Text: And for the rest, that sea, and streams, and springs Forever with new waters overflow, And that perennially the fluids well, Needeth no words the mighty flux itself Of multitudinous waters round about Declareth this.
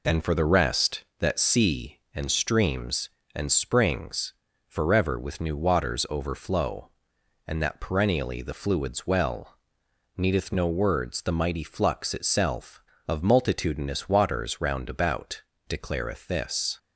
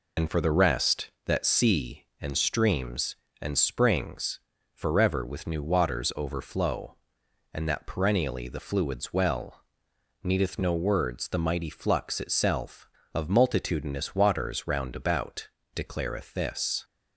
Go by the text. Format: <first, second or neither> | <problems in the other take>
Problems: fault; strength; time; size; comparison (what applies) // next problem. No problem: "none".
first | loses the start of "And"; at 0.1 s; 60 ms // pauses between "springs" and "Forever"; slight; at 4.4 s; 0.34 s long; slight in the first // pauses between "about" and "Declareth"; slight; at 15.4 s; 0.26 s long; slight in the first